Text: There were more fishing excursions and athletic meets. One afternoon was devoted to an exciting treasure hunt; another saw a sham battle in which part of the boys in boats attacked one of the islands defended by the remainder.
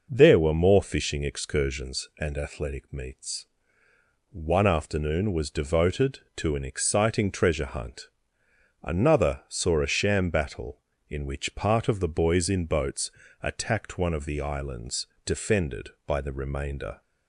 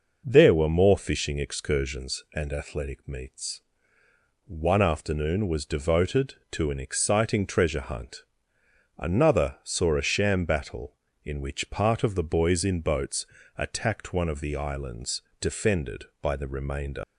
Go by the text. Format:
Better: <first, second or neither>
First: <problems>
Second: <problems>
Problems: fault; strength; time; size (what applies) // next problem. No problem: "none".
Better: first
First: pauses between "boats" and "attacked"; slight; at 13.1 s; 0.32 s long // pauses between "islands" and "defended"; slight; at 15.0 s; 0.20 s long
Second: pauses between "boats" and "attacked"; slight; at 13.2 s; 0.32 s long // pauses between "islands" and "defended"; slight; at 15.2 s; 0.20 s long // leaves "remainder" unfinished; at 17.0 s; 130 ms